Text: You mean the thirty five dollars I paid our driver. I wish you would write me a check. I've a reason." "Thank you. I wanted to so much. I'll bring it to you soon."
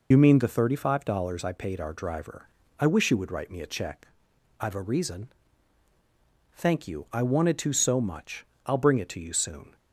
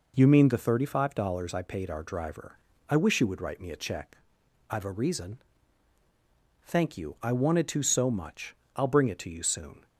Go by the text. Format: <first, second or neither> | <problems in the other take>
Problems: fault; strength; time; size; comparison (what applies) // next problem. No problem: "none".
second | loses the start of "You"; at 0.1 s; 65 ms